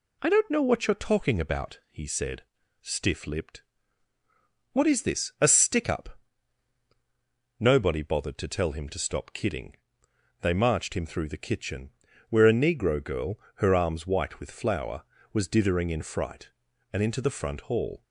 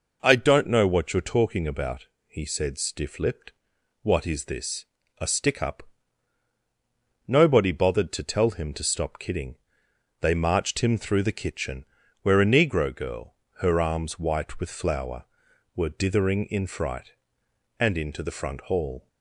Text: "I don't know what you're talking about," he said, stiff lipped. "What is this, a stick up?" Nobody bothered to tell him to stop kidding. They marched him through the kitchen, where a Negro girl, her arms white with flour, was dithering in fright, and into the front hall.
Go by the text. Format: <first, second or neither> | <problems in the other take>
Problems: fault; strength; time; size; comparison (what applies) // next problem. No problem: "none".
first | says "were" for "was"; at 15.7 s